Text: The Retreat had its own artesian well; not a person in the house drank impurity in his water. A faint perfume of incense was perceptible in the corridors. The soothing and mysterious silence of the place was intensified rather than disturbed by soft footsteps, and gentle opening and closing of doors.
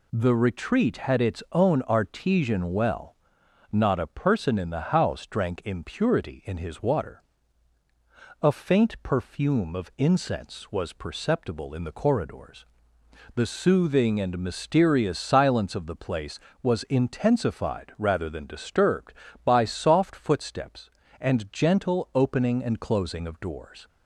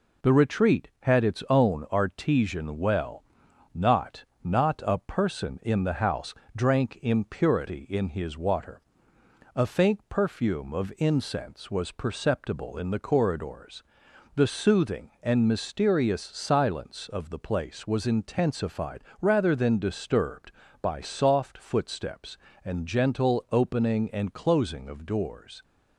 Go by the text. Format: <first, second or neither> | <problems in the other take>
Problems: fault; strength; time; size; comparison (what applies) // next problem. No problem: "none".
first | says "not" twice; at 4.4 s // pauses between "house" and "drank"; slight; at 6.3 s; 0.20 s long // pauses between "intensified" and "rather"; slight; at 19.0 s; 0.20 s long